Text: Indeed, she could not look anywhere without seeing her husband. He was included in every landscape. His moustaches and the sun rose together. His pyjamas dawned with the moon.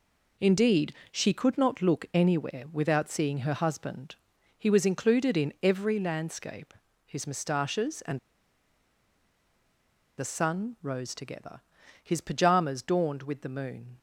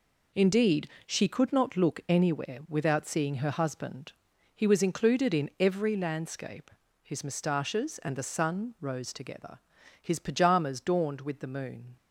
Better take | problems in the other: second | pauses between "and" and "the"; strong; at 8.1 s; 1.9 s long

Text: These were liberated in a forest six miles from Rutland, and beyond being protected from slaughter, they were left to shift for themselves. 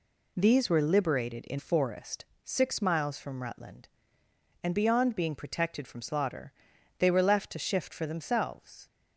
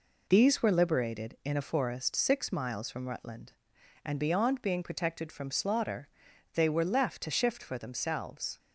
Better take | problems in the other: second | skips "a"; at 1.5 s // pauses between "forest" and "six"; slight; at 2.2 s; 0.22 s long

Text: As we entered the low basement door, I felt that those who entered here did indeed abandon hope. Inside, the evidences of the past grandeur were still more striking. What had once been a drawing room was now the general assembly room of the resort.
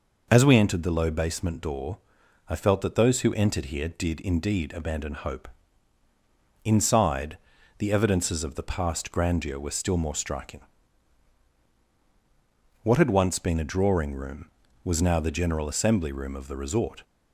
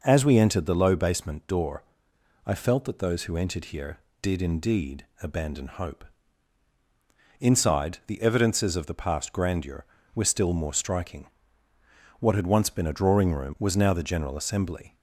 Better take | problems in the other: first | pauses between "indeed" and "abandon"; slight; at 5.0 s; 0.16 s long // stops before "room of the resort"; at 14.9 s

